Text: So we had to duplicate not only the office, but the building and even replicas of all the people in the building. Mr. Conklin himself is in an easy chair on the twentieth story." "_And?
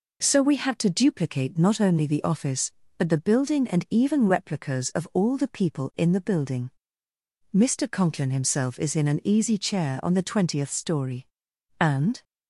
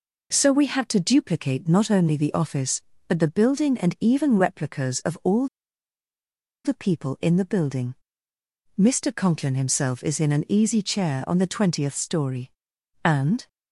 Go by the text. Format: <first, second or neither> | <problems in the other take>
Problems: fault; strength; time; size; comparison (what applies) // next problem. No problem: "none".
first | pauses between "all" and "the"; at 5.4 s; 1.1 s long